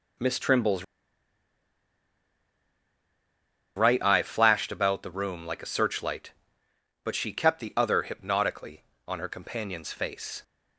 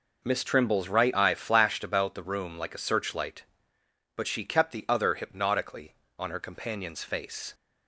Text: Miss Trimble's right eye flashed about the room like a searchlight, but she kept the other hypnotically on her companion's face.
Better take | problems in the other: second | pauses between "Trimble's" and "right"; strong; at 0.8 s; 2.9 s long

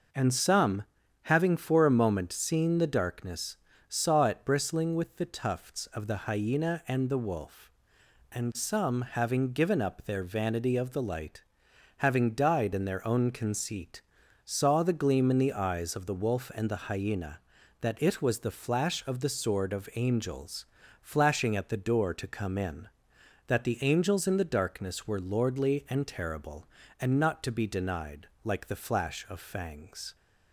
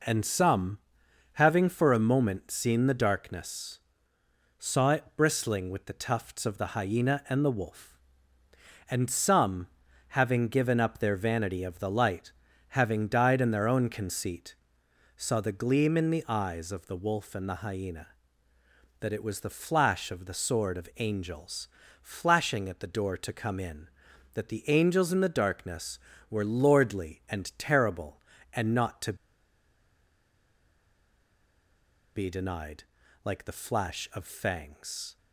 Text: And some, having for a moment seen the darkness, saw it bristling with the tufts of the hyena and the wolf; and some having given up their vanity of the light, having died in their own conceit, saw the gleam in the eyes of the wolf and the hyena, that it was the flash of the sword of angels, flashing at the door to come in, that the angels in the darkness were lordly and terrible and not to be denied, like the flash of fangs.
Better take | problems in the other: first | pauses between "some" and "having"; at 9.6 s; 0.42 s long // pauses between "to" and "be"; strong; at 29.1 s; 3.0 s long

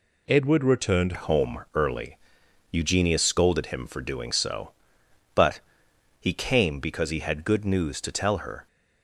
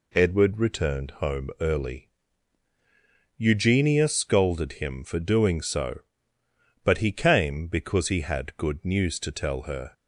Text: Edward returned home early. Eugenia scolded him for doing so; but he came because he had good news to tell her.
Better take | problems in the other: second | changes voice at "home"; from 1.1 s on; 7.5 s long // pauses between "but" and "he"; noticeable; at 5.6 s; 0.58 s long

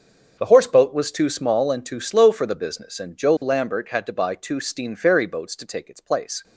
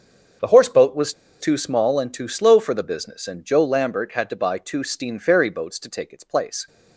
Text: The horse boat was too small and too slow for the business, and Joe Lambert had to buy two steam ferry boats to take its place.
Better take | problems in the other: first | starts louder than the rest; until 1.6 s; 6.5 dB; also in the first // pauses between "was" and "too"; slight; at 1.1 s; 0.28 s long

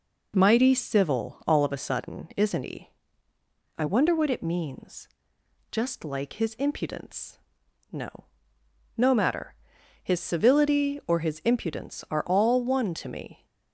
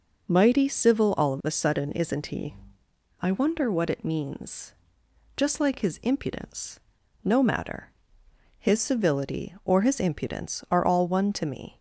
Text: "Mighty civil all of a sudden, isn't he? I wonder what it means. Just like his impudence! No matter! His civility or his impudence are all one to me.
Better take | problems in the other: second | says "No" twice; at 8.9 s

